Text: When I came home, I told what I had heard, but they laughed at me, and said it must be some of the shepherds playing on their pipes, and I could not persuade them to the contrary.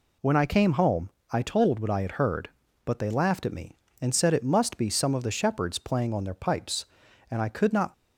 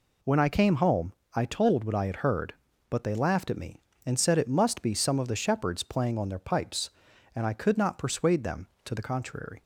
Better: second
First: stops before "persuade them to the contrary"; at 7.9 s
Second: none

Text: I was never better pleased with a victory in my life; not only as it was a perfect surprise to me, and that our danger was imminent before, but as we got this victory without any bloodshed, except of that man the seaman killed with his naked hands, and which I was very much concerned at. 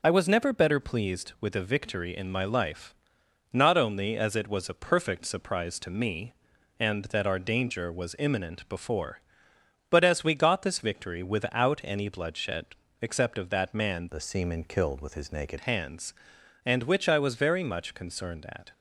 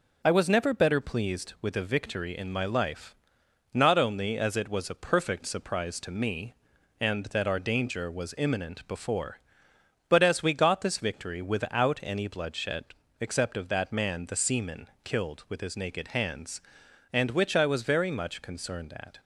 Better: second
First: changes voice from "the" to "naked"; from 14.0 to 15.5 s; 1.5 s long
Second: none

